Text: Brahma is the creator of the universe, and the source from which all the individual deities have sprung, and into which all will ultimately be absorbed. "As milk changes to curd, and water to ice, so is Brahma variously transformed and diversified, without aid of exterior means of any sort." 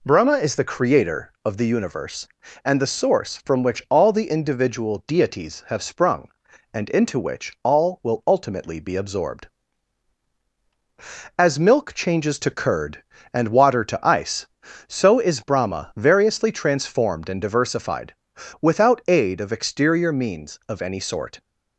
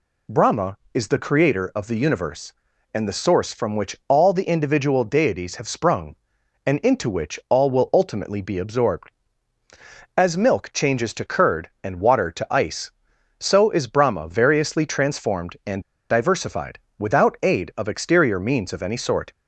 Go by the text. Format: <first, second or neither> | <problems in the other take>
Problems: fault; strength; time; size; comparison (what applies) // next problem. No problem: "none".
first | pauses between "and" and "diversified"; slight; at 15.8 s; 0.28 s long